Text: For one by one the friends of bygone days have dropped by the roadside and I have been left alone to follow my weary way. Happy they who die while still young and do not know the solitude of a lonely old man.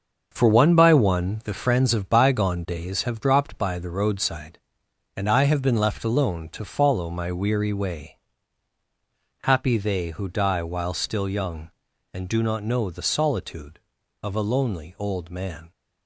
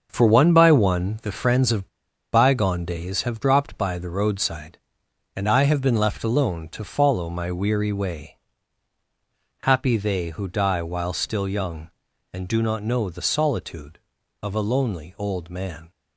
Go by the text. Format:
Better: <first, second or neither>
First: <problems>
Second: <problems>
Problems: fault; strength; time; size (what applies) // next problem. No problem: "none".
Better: first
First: starts louder than the rest; until 1.3 s; 7 dB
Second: starts louder than the rest; until 1.1 s; 7 dB // pauses between "of" and "bygone"; noticeable; at 1.8 s; 0.46 s long